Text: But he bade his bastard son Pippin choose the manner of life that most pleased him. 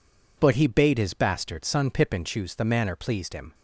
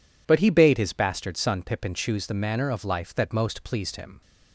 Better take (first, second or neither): second